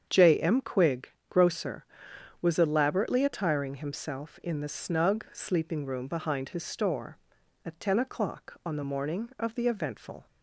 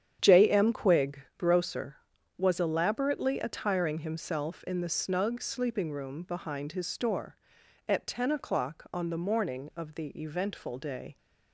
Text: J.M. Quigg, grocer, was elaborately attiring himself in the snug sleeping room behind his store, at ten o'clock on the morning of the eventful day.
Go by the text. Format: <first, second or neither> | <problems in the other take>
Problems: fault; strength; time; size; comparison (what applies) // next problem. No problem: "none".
second | starts louder than the rest; strong; until 1.1 s; 8 dB; strong in the second // stops before "day"; at 10.2 s